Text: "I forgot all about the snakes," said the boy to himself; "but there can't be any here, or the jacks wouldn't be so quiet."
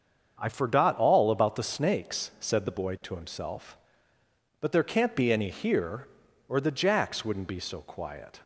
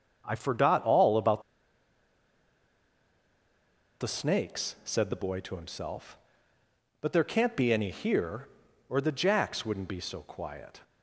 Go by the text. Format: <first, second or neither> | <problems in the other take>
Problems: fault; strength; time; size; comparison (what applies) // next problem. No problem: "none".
first | starts louder than the rest; until 1.2 s; 7 dB; also in the first // pauses between "about" and "the"; strong; at 1.4 s; 2.5 s long